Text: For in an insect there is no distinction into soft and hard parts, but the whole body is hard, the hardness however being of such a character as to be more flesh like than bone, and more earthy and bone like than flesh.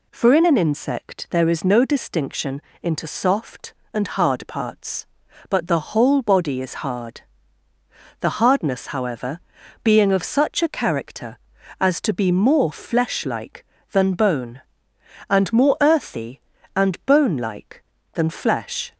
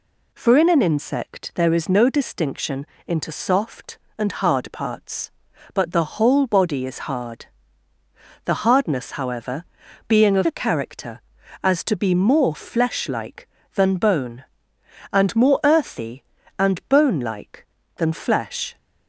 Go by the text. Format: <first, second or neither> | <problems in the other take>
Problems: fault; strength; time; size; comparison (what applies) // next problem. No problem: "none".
first | pauses between "distinction" and "into"; slight; at 2.8 s; 0.20 s long; slight in the first // pauses between "however" and "being"; at 9.6 s; 0.44 s long; also in the first // skips "such"; at 10.4 s